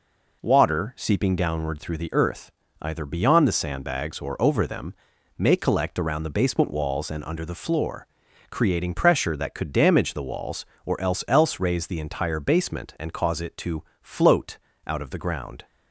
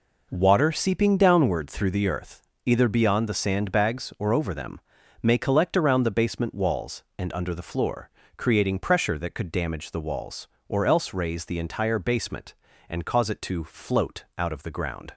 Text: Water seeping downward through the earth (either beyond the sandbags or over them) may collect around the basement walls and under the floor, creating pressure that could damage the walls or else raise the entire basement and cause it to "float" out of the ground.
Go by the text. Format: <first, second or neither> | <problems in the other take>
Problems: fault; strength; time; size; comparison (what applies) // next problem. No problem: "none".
second | says "else" twice; at 11.2 s // pauses between "to" and "float"; slight; at 13.8 s; 0.18 s long // pauses between "float" and "out"; slight; at 14.5 s; 0.28 s long